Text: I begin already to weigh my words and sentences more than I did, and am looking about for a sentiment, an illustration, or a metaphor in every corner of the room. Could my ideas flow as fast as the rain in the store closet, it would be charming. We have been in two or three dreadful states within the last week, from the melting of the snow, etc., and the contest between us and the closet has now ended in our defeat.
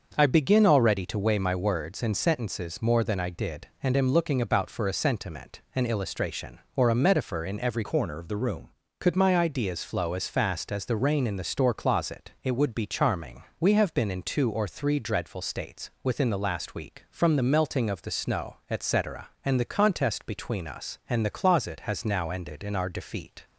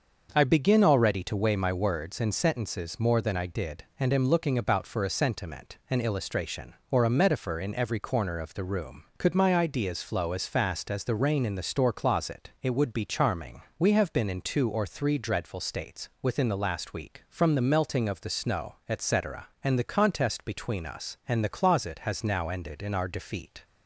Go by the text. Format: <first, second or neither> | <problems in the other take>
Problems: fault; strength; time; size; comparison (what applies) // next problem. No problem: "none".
second | starts louder than the rest; until 1.1 s; 6.5 dB; also in the second // changes voice from "corner" to "room"; from 7.8 to 8.6 s; 0.8 s long